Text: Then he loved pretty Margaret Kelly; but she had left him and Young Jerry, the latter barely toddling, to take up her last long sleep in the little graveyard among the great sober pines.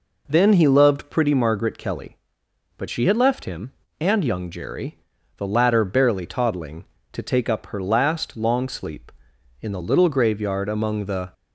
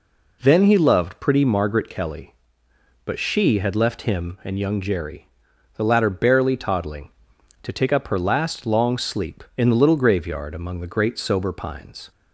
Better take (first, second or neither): second